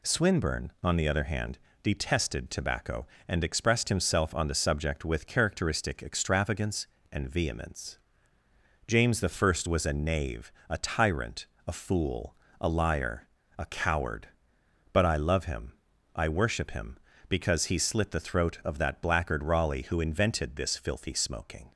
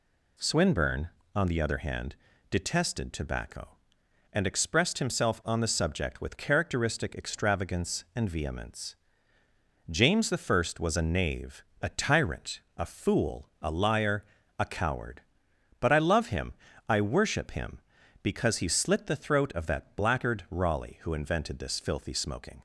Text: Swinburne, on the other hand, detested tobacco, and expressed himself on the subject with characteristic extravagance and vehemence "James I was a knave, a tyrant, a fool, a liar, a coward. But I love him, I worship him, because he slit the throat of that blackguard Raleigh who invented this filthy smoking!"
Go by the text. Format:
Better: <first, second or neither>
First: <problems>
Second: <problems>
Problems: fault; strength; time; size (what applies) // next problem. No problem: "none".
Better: neither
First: pauses between "vehemence" and "James"; noticeable; at 7.9 s; 0.88 s long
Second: pauses between "vehemence" and "James"; noticeable; at 8.9 s; 0.94 s long